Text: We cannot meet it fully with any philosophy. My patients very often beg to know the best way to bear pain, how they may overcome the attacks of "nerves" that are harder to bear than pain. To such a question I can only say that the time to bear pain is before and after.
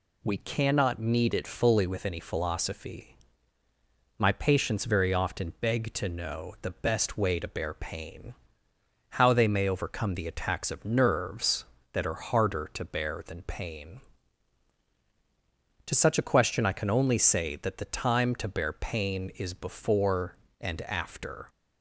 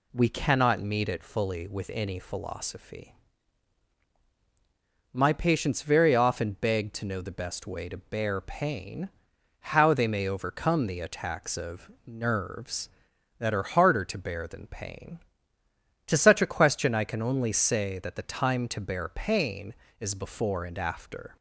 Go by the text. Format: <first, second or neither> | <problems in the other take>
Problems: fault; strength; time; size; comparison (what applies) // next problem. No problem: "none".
neither | none